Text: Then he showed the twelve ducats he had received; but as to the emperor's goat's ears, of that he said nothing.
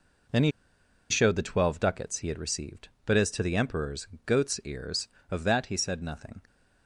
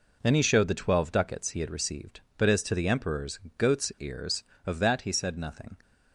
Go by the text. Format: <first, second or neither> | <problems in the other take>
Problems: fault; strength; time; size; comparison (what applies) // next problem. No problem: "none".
second | pauses between "he" and "showed"; noticeable; at 0.5 s; 0.59 s long // pauses between "emperor's" and "goat's"; slight; at 4.0 s; 0.16 s long; slight in the second